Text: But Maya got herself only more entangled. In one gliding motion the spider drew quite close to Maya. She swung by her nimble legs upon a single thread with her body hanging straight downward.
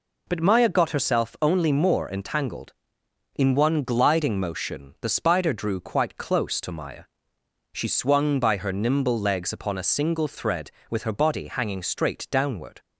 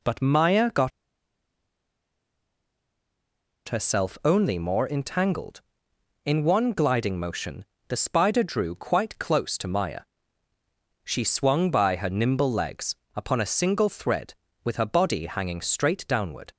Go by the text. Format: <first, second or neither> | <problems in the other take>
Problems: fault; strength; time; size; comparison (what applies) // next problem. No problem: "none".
first | pauses between "got" and "herself"; strong; at 0.9 s; 2.7 s long // pauses between "motion" and "the"; slight; at 7.6 s; 0.24 s long // pauses between "legs" and "upon"; slight; at 12.9 s; 0.18 s long